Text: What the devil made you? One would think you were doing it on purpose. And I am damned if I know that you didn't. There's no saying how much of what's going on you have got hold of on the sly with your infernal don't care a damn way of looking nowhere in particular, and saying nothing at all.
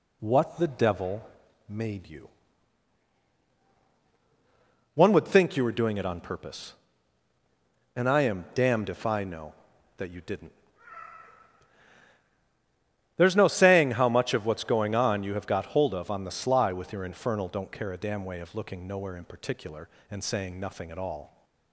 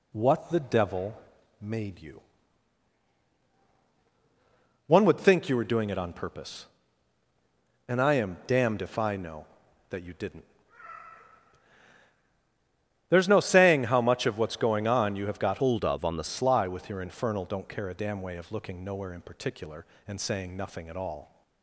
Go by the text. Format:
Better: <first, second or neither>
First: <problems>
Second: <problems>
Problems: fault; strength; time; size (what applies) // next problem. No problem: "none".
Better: first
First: pauses between "devil" and "made"; at 1.2 s; 0.40 s long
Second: pauses between "devil" and "made"; at 1.1 s; 0.40 s long // changes voice from "hold" to "the"; from 15.5 to 16.2 s; 0.7 s long